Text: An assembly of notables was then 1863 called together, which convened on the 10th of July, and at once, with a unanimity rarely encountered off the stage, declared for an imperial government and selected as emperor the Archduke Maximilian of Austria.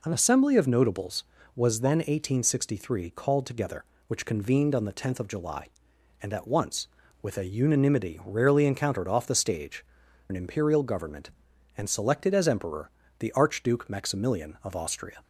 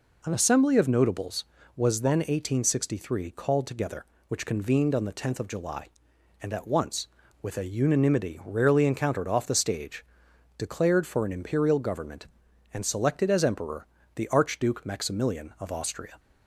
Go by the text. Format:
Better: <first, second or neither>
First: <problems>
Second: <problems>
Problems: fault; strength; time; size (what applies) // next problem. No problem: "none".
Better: second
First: skips "declared for"; at 10.0 s // pauses between "emperor" and "the"; slight; at 12.8 s; 0.30 s long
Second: pauses between "emperor" and "the"; slight; at 13.8 s; 0.30 s long